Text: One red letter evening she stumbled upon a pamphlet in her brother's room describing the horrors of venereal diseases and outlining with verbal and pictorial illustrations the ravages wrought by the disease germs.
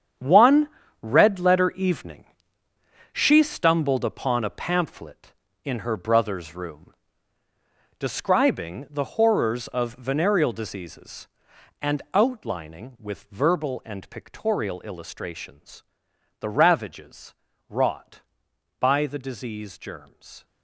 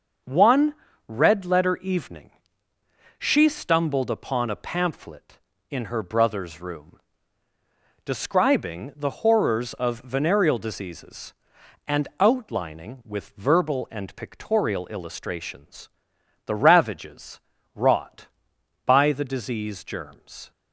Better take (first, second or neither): second